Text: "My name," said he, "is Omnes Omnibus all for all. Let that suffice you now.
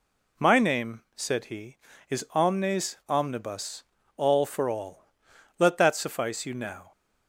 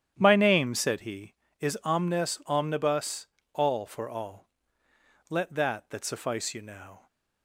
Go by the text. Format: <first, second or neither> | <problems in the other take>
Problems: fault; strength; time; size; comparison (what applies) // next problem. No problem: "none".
first | starts louder than the rest; strong; until 1.1 s; 10 dB // pauses between "Omnibus" and "all"; slight; at 3.2 s; 0.28 s long; slight in the first // says "that" twice; at 5.8 s